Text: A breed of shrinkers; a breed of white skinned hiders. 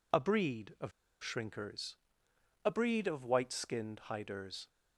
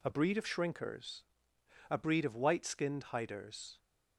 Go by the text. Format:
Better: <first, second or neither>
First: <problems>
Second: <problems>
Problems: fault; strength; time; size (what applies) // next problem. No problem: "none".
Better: second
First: pauses between "of" and "shrinkers"; slight; at 0.9 s; 0.32 s long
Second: none